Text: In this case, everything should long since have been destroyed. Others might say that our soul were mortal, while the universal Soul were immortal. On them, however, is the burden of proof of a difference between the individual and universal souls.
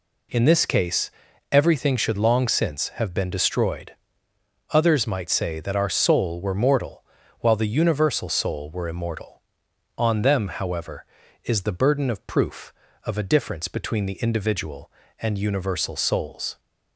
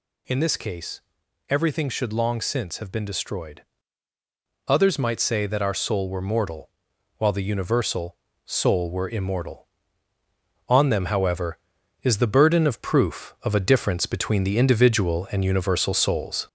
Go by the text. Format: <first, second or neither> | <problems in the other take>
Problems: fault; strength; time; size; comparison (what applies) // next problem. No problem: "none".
first | gets louder; throughout; 3.5 dB // pauses between "universal" and "Soul"; slight; at 8.1 s; 0.32 s long